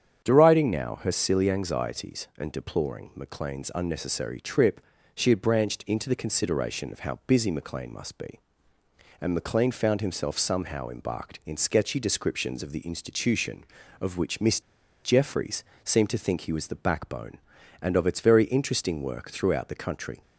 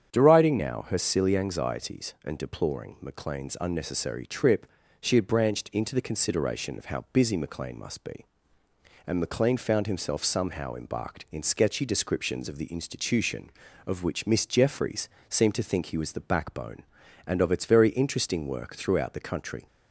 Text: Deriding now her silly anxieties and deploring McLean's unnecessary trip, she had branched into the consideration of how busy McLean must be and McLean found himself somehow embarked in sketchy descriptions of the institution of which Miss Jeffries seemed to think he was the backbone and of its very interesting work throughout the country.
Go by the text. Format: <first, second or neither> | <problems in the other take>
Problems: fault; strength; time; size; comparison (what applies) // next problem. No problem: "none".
second | starts louder than the rest; strong; until 1.2 s; 8 dB; strong in the second // pauses between "Miss" and "Jeffries"; at 14.6 s; 0.43 s long // pauses between "Jeffries" and "seemed"; slight; at 15.6 s; 0.18 s long; slight in the second